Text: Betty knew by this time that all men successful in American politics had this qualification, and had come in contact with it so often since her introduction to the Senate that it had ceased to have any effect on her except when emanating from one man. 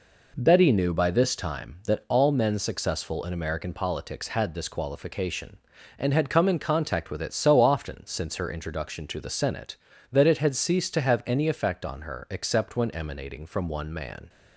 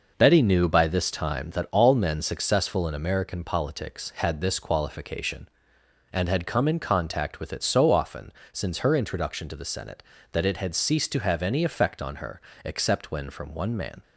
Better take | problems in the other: first | pauses between "often" and "since"; slight; at 8.3 s; 0.20 s long // pauses between "her" and "except"; slight; at 12.3 s; 0.24 s long // skips "emanating"; at 13.2 s

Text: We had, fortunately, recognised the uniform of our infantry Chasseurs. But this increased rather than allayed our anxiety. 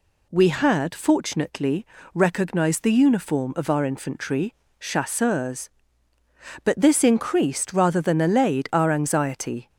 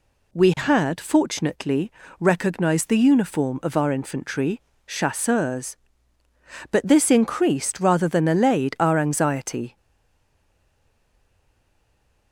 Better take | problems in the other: first | pauses between "infantry" and "Chasseurs"; slight; at 4.6 s; 0.24 s long; slight in the first // stays silent after the last word; strong; from 9.7 s on; 2.6 s long

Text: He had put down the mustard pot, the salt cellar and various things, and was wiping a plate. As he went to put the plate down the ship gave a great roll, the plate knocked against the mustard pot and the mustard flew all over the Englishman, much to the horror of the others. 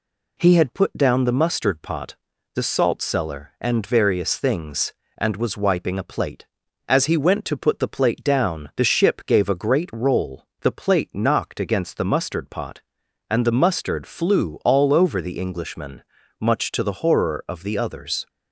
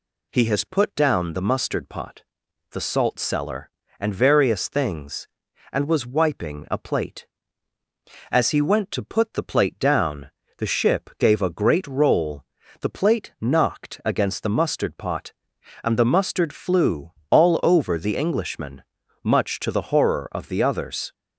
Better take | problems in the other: first | says "has" for "had"; at 0.4 s // pauses between "down" and "the"; slight; at 10.3 s; 0.28 s long // pauses between "flew" and "all"; slight; at 17.1 s; 0.20 s long

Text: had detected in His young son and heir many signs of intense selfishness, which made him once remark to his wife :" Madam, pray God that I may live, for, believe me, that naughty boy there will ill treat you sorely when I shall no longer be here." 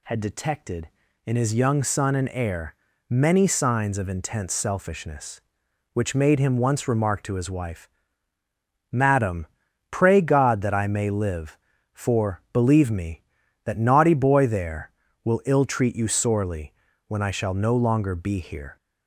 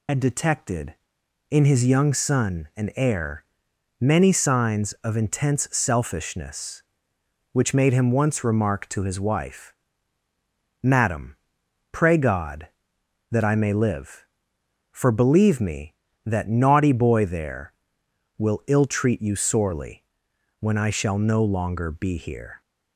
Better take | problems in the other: first | loses the start of "had"; at 0.0 s; 65 ms // pauses between "heir" and "many"; noticeable; at 3.4 s; 0.56 s long; slight in the first // pauses between "sorely" and "when"; noticeable; at 20.0 s; 0.56 s long; slight in the first

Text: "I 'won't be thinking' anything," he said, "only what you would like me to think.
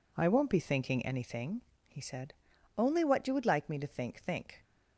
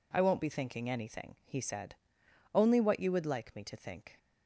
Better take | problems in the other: second | says "think" twice; at 4.2 s

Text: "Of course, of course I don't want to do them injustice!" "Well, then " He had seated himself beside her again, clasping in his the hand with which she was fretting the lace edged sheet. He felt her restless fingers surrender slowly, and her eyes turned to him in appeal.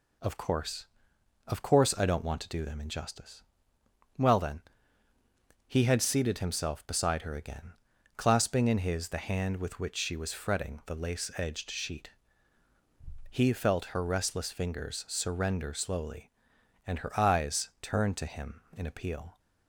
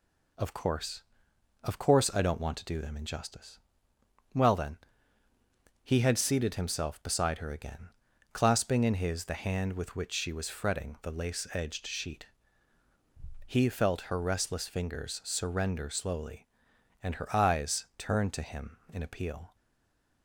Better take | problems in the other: first | stays silent after the last word; slight; from 19.5 s on; 0.7 s long

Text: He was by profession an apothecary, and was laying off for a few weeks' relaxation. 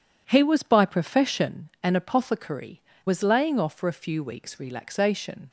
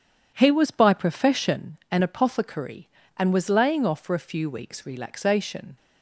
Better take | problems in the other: second | skips "and"; at 2.9 s

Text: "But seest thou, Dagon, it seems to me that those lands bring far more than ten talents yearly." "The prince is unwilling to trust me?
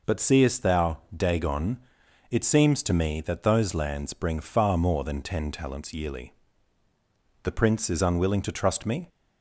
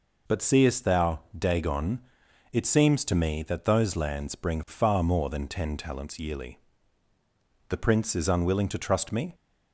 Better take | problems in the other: neither | none

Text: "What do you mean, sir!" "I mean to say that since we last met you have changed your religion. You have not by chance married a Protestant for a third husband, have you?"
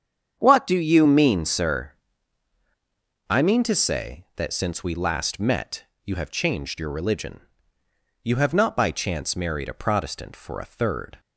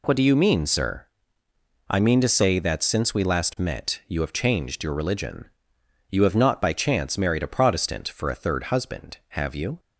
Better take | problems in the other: second | starts louder than the rest; strong; until 1.4 s; 8 dB // pauses between "met" and "you"; slight; at 5.8 s; 0.20 s long // stops before "husband have you"; at 11.1 s

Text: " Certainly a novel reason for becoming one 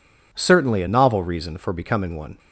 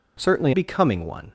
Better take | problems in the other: first | skips "a novel reason for"; at 0.5 s

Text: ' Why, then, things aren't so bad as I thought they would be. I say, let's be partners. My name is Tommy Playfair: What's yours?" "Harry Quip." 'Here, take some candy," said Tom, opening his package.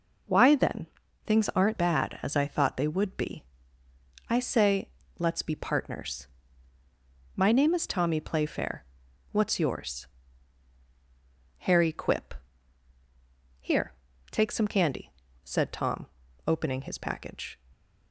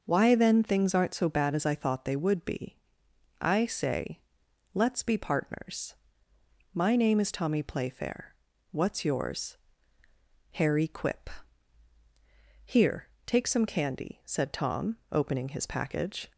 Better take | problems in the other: second | skips "so"; at 1.7 s

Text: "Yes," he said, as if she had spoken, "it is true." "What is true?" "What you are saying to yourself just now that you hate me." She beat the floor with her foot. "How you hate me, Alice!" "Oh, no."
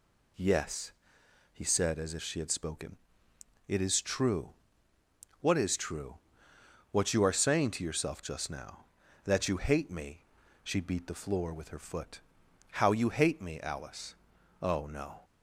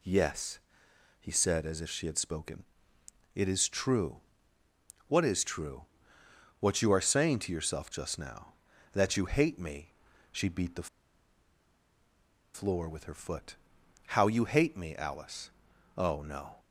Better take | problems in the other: first | pauses between "the" and "floor"; strong; at 10.8 s; 1.6 s long

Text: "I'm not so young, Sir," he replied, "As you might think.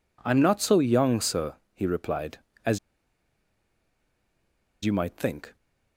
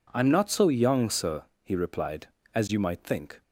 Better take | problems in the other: second | pauses between "As" and "you"; strong; at 2.7 s; 2.0 s long

